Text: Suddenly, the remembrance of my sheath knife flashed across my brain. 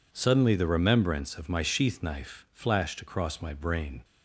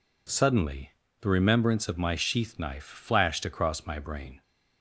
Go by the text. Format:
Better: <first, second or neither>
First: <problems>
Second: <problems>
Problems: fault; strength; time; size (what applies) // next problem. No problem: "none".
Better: neither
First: none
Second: none